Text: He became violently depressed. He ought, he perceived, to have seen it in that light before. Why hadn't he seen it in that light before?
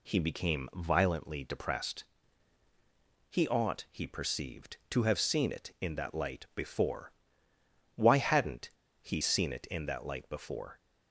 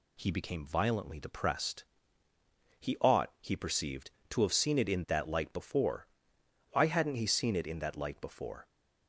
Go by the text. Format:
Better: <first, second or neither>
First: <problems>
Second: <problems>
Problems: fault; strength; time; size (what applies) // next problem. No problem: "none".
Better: second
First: pauses between "hadn't" and "he"; slight; at 8.7 s; 0.30 s long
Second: none